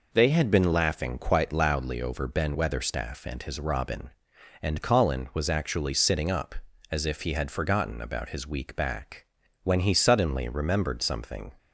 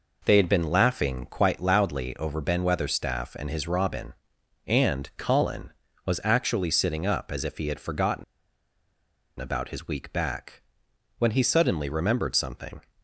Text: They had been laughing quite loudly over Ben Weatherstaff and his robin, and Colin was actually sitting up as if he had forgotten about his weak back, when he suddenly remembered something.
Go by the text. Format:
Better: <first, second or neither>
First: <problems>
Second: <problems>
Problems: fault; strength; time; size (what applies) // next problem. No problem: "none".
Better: first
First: none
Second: pauses between "forgotten" and "about"; at 8.2 s; 1.1 s long